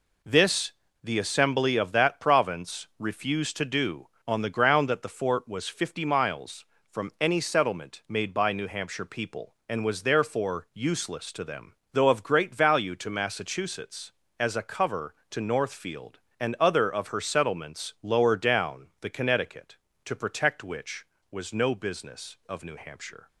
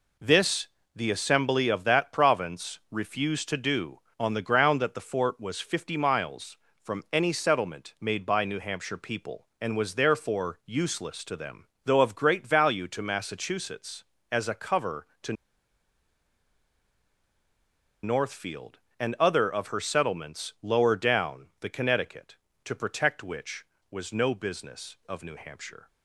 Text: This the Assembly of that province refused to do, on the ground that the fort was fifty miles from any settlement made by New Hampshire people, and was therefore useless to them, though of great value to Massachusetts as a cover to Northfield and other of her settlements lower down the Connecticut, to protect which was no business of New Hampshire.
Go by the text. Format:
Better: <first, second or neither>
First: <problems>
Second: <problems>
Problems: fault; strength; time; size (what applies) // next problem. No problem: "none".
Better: first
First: pauses between "This" and "the"; slight; at 0.7 s; 0.31 s long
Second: pauses between "This" and "the"; slight; at 0.6 s; 0.28 s long // pauses between "to" and "Northfield"; strong; at 15.3 s; 2.6 s long